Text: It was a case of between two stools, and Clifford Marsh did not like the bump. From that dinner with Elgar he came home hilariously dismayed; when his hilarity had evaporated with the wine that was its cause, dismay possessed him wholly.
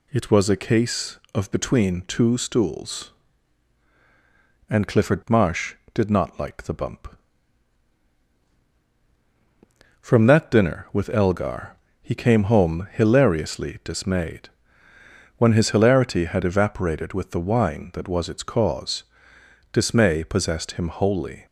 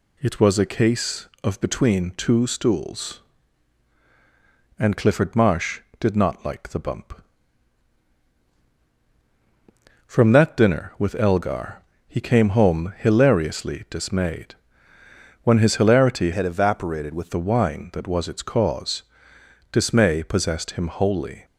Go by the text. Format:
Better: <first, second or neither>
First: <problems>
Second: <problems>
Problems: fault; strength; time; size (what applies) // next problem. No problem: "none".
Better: first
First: pauses between "Elgar" and "he"; slight; at 11.7 s; 0.24 s long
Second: pauses between "Elgar" and "he"; slight; at 11.8 s; 0.24 s long // changes voice from "had" to "with"; from 16.3 to 17.2 s; 0.9 s long